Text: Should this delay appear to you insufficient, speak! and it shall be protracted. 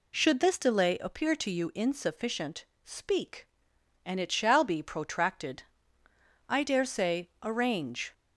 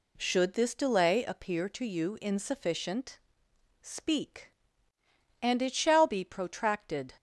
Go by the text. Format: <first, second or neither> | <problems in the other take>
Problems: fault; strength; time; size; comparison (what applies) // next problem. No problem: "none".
second | goes on to say "I dare say arrange"; from 6.4 s on; 1.6 s long